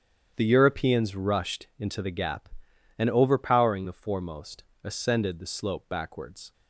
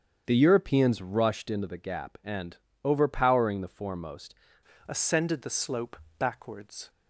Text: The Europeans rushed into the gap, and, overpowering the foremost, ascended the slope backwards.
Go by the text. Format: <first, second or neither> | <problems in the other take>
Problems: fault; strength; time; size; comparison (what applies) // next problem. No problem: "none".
first | starts louder than the rest; strong; until 1.2 s; 7.5 dB; strong in the first // changes voice at "ascended"; from 4.8 s on; 2.0 s long // pauses between "slope" and "backwards"; slight; at 5.9 s; 0.20 s long